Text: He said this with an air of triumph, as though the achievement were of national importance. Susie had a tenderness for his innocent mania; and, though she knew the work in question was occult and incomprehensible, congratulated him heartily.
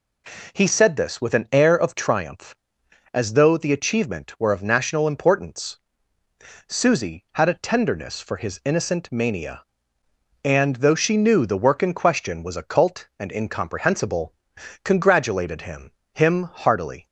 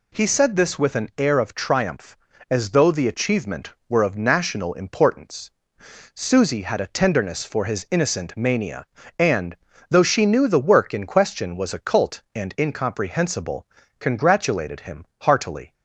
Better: second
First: says "him" twice; at 16.1 s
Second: none

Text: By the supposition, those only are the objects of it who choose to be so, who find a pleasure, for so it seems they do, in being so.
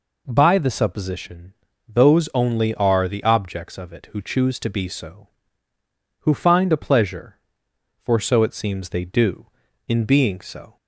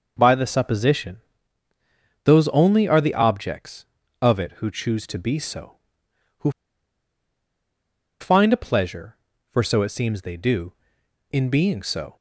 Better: first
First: none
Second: pauses between "who" and "find"; strong; at 6.4 s; 1.7 s long

